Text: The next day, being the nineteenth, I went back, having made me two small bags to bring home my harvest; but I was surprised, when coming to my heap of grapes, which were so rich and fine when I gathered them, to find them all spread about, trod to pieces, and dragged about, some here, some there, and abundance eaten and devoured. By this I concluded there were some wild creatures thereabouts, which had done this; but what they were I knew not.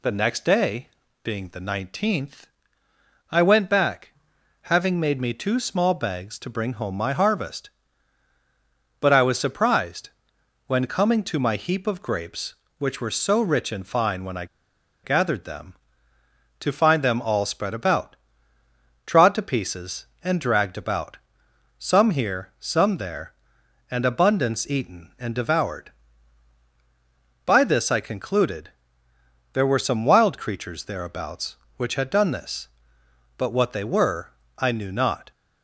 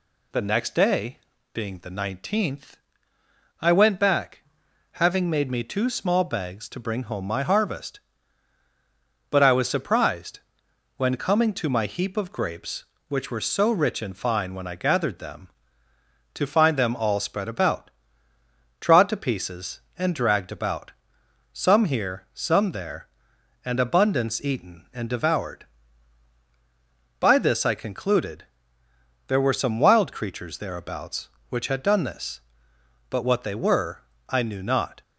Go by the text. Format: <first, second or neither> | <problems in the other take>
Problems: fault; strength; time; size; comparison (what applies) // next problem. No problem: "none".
second | pauses between "I" and "gathered"; noticeable; at 14.4 s; 0.58 s long // pauses between "concluded" and "there"; noticeable; at 28.7 s; 0.82 s long; noticeable in the second // pauses between "were" and "I"; slight; at 34.3 s; 0.26 s long; slight in the second